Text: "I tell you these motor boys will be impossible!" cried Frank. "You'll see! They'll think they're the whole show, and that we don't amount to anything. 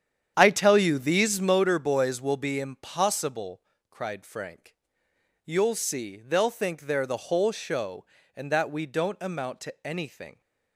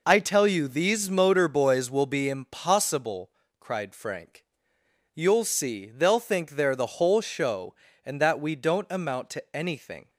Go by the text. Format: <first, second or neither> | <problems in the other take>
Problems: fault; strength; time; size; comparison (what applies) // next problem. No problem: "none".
second | starts louder than the rest; strong; until 1.7 s; 9 dB